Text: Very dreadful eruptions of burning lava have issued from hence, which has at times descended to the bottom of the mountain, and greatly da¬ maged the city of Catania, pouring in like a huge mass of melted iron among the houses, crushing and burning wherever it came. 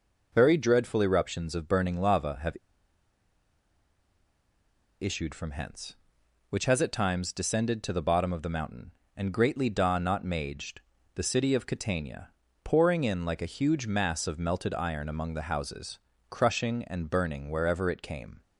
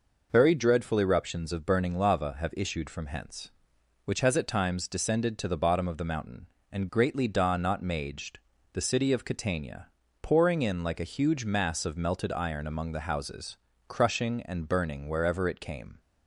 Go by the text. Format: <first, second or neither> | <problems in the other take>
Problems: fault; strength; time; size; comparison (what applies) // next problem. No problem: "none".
second | pauses between "have" and "issued"; strong; at 2.5 s; 2.4 s long // pauses between "maged" and "the"; slight; at 10.7 s; 0.34 s long; slight in the second